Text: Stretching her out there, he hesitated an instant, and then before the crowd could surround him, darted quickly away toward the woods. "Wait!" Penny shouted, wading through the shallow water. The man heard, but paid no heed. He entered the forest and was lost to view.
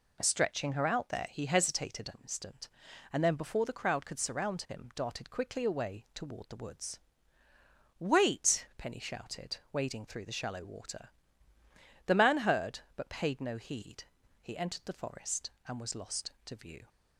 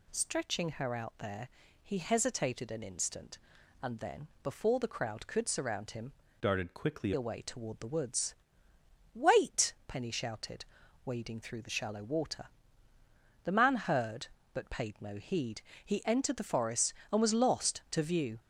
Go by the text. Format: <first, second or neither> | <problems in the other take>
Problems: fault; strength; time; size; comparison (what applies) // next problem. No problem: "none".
first | pauses between "then" and "before"; slight; at 4.2 s; 0.16 s long // changes voice from "darted" to "quickly"; from 6.4 to 7.1 s; 0.7 s long